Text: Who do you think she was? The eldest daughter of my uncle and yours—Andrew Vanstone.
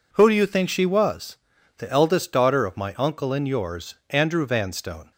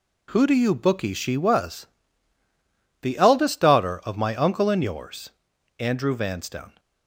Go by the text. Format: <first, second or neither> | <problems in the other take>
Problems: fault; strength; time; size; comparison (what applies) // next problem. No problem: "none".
first | says "bookie" for "think"; at 0.7 s